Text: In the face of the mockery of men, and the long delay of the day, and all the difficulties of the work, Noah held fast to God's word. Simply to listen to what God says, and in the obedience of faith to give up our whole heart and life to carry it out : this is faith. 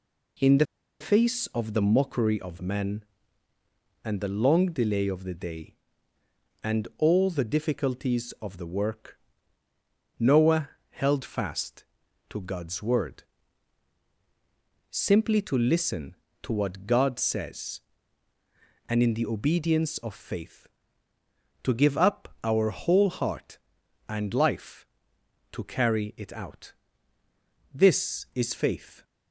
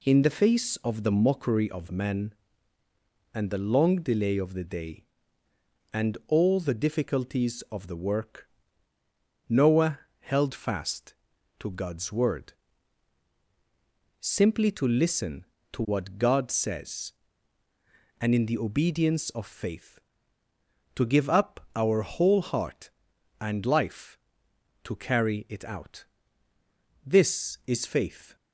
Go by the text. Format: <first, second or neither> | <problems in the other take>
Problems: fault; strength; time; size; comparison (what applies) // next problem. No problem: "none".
second | pauses between "the" and "face"; slight; at 0.6 s; 0.35 s long // pauses between "Noah" and "held"; slight; at 10.6 s; 0.22 s long; slight in the second